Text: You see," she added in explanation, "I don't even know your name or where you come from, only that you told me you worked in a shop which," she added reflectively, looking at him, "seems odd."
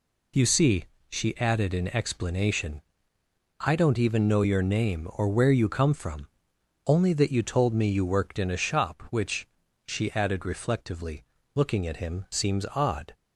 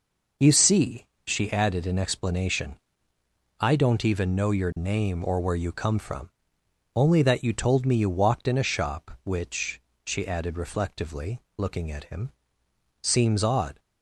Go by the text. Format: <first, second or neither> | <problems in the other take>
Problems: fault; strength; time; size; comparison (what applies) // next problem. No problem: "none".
first | says "walked" for "worked"; at 8.0 s